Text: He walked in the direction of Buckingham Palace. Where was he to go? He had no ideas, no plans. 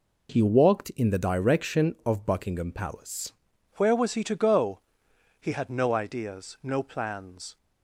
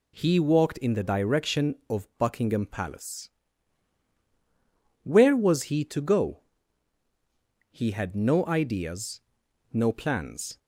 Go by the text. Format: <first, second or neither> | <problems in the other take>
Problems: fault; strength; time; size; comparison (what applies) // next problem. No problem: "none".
second | changes voice at "Where"; from 3.7 s on; 3.8 s long